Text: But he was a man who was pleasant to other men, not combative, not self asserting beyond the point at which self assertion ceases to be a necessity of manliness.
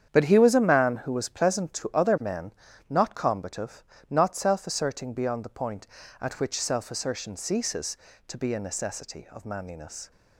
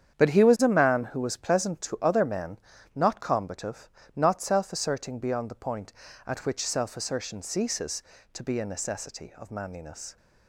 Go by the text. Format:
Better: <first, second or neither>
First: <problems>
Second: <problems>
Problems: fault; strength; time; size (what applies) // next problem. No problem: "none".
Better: neither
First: starts louder than the rest; strong; until 1.1 s; 8.5 dB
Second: starts louder than the rest; strong; until 1.2 s; 8.5 dB